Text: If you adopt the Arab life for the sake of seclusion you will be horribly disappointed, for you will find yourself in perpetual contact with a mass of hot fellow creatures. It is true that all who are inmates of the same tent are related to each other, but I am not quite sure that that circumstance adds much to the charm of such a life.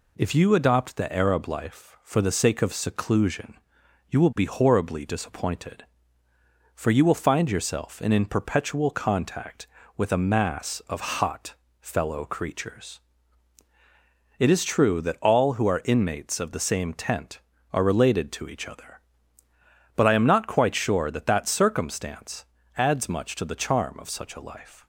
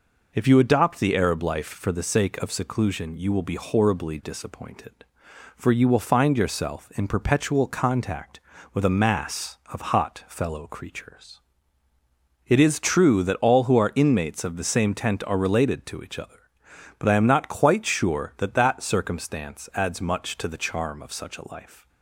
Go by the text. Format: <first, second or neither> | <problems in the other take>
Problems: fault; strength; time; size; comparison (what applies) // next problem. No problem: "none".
second | pauses between "seclusion" and "you"; noticeable; at 3.5 s; 0.50 s long // says "in" twice; at 8.1 s // pauses between "hot" and "fellow"; slight; at 11.5 s; 0.26 s long // pauses between "circumstance" and "adds"; slight; at 22.4 s; 0.34 s long